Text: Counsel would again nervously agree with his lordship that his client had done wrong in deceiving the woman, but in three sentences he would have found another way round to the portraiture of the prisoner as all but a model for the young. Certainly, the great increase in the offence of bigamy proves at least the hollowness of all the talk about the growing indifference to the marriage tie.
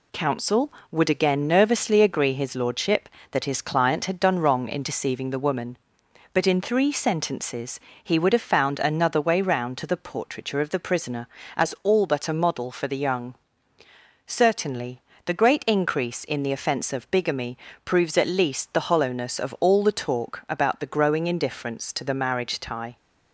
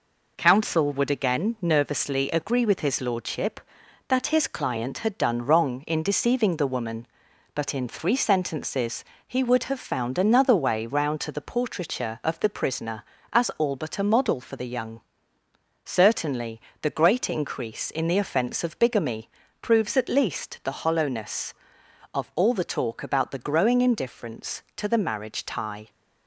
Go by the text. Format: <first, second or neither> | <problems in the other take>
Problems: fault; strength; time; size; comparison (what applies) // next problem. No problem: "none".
second | skips "with"; at 2.3 s // pauses between "sentences" and "he"; slight; at 7.7 s; 0.22 s long; slight in the second // pauses between "bigamy" and "proves"; slight; at 17.5 s; 0.30 s long; slight in the second